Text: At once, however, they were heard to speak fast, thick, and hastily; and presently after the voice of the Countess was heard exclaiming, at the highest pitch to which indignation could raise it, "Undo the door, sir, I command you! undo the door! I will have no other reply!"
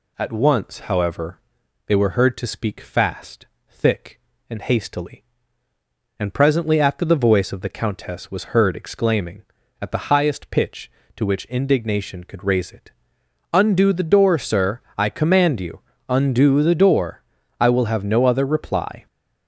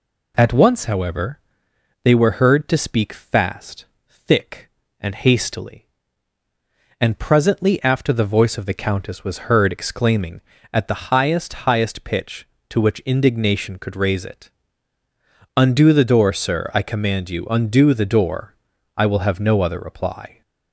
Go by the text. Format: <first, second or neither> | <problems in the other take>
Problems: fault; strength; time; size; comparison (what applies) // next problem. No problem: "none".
first | says "highest" twice; at 11.6 s